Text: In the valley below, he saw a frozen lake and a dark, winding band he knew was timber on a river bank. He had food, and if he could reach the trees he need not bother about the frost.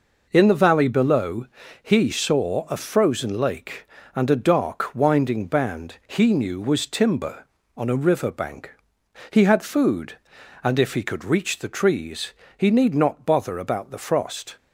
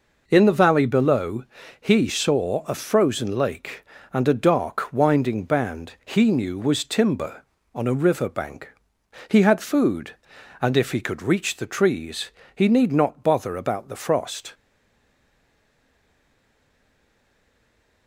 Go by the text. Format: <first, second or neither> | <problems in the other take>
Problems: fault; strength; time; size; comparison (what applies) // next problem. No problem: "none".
first | pauses between "trees" and "he"; slight; at 12.3 s; 0.24 s long; slight in the first // stays silent after the last word; strong; from 14.5 s on; 3.5 s long